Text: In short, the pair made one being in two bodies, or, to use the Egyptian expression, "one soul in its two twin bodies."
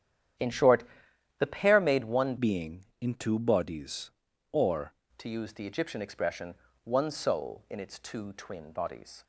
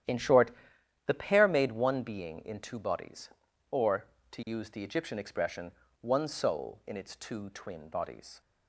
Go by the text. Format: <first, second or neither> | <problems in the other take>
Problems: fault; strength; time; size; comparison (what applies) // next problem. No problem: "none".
second | starts louder than the rest; strong; until 1.9 s; 10 dB; strong in the second // changes voice from "being" to "or"; from 2.3 to 4.9 s; 2.6 s long